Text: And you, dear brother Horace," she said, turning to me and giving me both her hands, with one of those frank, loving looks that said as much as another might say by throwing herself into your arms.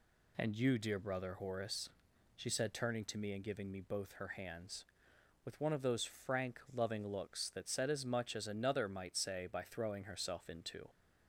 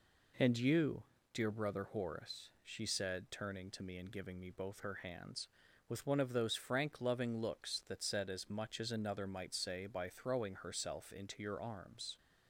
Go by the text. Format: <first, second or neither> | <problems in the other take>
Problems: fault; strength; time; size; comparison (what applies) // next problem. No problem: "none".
second | stops before "your arms"; at 10.8 s